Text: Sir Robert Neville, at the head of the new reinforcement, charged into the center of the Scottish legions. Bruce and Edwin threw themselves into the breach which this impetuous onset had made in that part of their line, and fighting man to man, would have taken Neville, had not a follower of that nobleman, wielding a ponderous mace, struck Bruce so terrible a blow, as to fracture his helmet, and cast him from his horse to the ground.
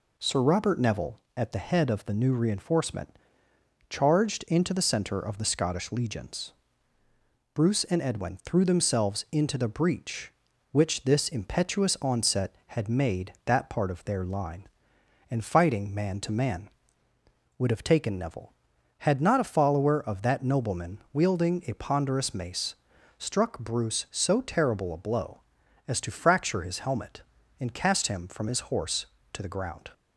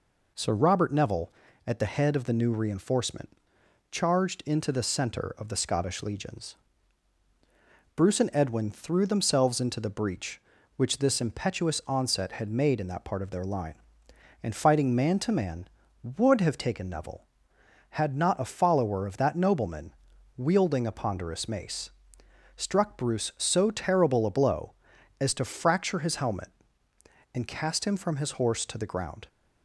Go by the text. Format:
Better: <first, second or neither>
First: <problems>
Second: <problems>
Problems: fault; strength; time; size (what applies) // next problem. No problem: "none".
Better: second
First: skips "in"; at 13.3 s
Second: none